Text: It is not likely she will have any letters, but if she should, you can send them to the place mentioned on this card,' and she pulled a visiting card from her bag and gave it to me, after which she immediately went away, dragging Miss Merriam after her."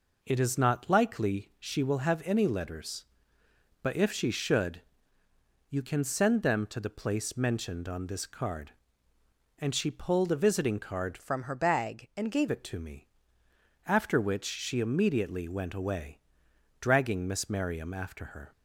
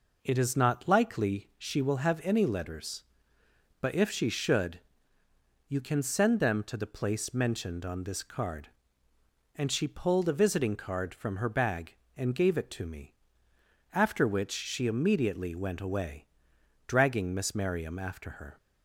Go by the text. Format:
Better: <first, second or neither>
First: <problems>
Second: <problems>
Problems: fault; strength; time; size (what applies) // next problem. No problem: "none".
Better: second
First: changes voice from "from" to "gave"; from 11.2 to 12.4 s; 1.2 s long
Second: none